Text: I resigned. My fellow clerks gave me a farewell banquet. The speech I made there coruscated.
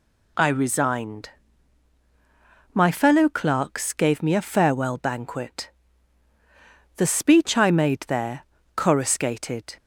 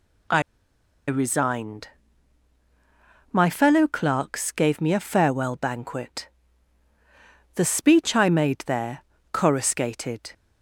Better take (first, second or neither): first